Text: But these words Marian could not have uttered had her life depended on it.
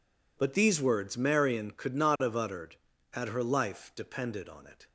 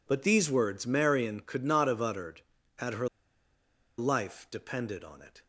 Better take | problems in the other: first | pauses between "her" and "life"; noticeable; at 3.0 s; 0.91 s long

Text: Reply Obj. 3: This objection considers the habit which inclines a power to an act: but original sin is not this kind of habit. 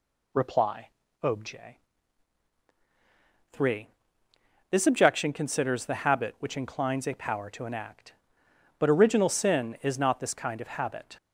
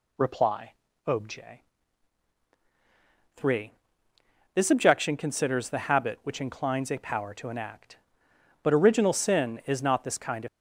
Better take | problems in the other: first | pauses between "Reply" and "Obj"; slight; at 0.7 s; 0.32 s long; slight in the first // stops before "habit"; at 10.4 s

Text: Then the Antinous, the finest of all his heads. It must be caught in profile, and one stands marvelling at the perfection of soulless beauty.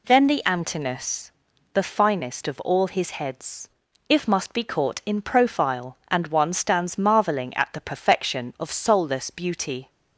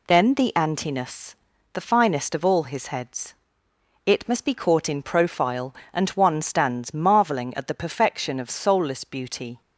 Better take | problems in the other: second | says "If" for "It"; at 4.0 s

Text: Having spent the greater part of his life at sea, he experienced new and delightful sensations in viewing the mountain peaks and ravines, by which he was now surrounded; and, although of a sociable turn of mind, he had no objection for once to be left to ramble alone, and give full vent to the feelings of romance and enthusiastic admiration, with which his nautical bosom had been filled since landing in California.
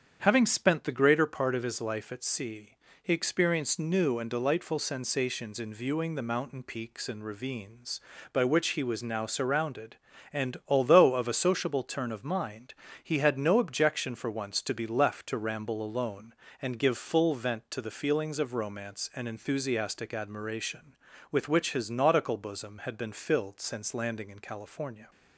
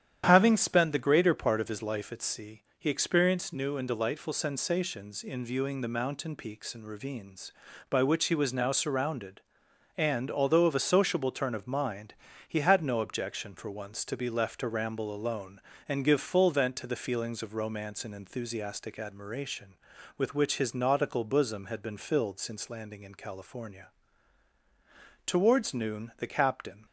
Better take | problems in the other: first | starts louder than the rest; strong; until 1.2 s; 10 dB; strong in the first // goes on to say "Towards noon the captain"; from 25.2 s on; 1.6 s long

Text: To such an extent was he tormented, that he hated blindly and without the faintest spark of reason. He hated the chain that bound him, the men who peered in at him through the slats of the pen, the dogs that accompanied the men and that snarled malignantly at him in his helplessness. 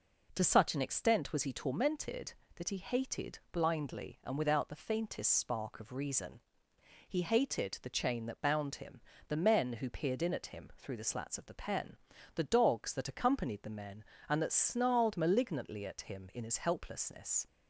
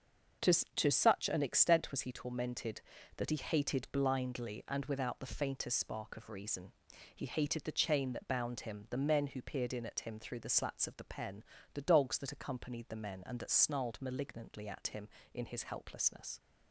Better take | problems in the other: first | starts louder than the rest; until 1.6 s; 6.5 dB // says "To" twice; at 0.7 s

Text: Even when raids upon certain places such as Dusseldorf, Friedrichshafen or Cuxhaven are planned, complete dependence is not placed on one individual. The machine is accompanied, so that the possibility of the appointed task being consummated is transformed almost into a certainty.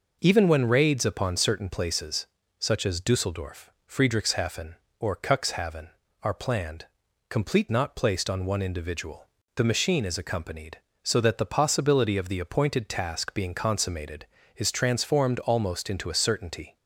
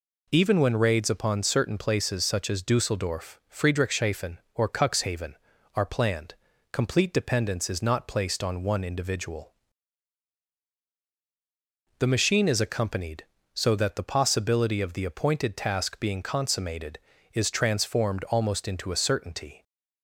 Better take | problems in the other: second | pauses between "places" and "such"; slight; at 2.2 s; 0.32 s long // skips "dependence is"; at 7.6 s

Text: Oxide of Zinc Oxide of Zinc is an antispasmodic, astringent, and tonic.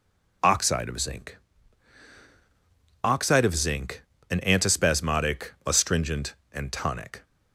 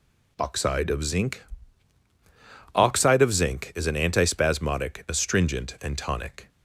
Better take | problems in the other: second | pauses between "Zinc" and "Oxide"; strong; at 1.3 s; 1.6 s long; strong in the second // skips "is"; at 4.1 s

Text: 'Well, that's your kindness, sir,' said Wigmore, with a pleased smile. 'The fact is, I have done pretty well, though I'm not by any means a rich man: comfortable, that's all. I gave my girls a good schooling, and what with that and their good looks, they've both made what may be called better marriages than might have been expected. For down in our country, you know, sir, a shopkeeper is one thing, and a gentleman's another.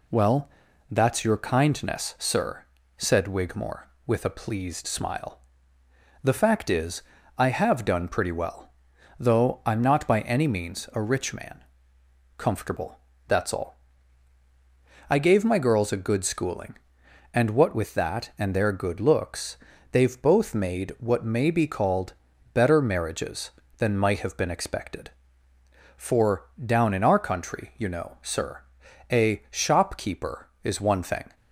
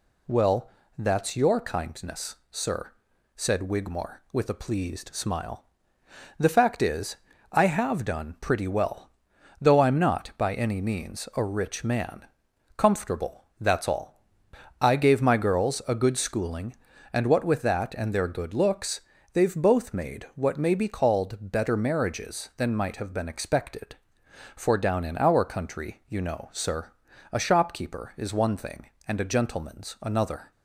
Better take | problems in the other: second | pauses between "called" and "better"; at 22.1 s; 0.40 s long // pauses between "For" and "down"; slight; at 26.4 s; 0.16 s long // stops before "and a gentleman's another"; at 31.3 s

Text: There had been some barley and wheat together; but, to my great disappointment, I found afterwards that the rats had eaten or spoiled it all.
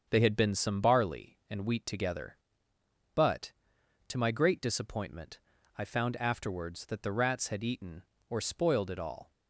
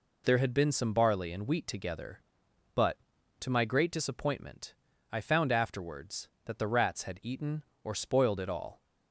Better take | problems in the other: second | starts louder than the rest; strong; until 1.1 s; 7 dB // says "They" for "There"; at 0.0 s

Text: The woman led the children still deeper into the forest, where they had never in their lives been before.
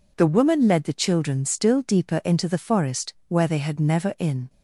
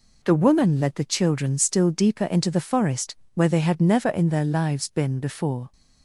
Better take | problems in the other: second | stops before "their lives been before"; at 4.4 s

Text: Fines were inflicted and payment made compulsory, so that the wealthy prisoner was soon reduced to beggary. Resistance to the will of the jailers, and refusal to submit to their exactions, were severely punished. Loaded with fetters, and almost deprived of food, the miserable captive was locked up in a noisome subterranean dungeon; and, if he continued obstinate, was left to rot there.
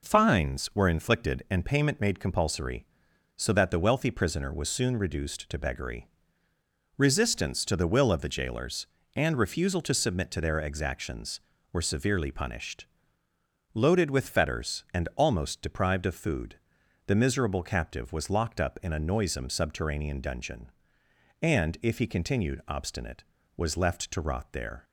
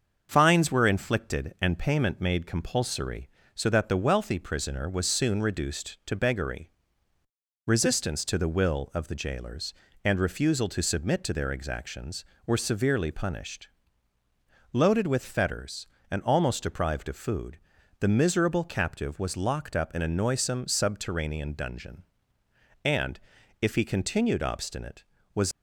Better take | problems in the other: first | starts louder than the rest; until 1.3 s; 6.5 dB // stops before "left to rot there"; at 25.5 s

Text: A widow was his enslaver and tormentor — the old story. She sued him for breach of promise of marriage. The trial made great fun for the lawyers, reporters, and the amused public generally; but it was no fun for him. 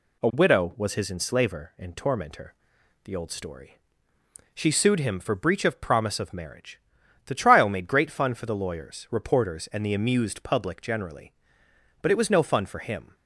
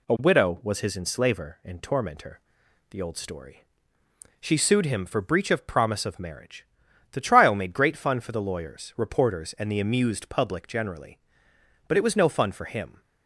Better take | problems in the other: neither | none

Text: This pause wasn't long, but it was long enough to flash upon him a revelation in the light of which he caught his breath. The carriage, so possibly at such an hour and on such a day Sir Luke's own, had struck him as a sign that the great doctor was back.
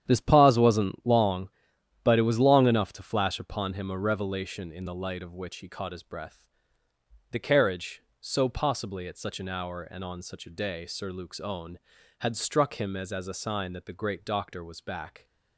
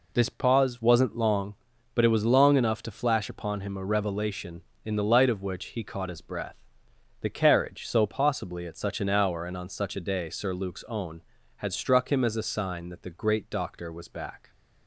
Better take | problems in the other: second | starts louder than the rest; strong; until 1.0 s; 9.5 dB // says "as" twice; at 13.1 s

